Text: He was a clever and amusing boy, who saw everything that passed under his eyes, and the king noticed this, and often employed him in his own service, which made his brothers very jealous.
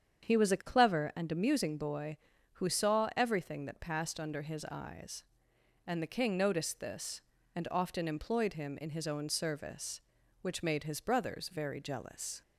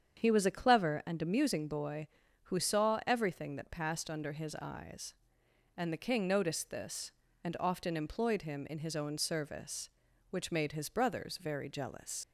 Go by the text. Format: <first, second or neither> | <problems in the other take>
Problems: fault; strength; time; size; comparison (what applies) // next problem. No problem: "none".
first | starts louder than the rest; strong; until 1.2 s; 8 dB; strong in the first // leaves "jealous" unfinished; at 12.2 s; 65 ms